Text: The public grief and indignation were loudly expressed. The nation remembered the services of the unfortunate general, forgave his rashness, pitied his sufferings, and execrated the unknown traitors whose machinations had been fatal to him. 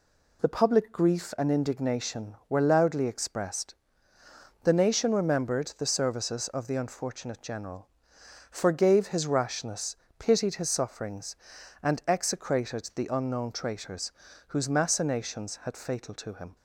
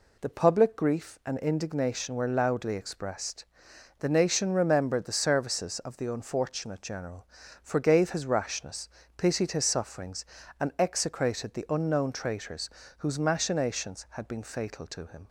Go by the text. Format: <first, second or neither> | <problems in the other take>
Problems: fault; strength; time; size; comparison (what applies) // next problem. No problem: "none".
second | pauses between "traitors" and "whose"; slight; at 14.1 s; 0.34 s long; slight in the second // skips "been"; at 15.7 s